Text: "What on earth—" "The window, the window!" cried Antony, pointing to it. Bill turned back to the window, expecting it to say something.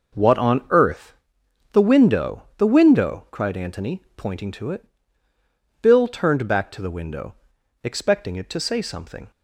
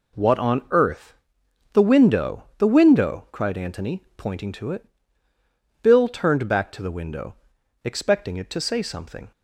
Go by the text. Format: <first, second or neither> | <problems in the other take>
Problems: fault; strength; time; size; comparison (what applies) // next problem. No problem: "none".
second | starts louder than the rest; noticeable; until 1.3 s; 6 dB